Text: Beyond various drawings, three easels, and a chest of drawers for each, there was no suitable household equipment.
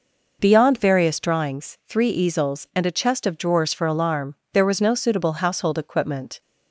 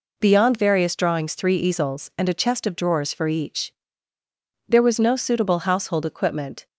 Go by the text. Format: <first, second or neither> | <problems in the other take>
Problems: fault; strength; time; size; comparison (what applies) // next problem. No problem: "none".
second | says "alarm" for "each"; at 3.8 s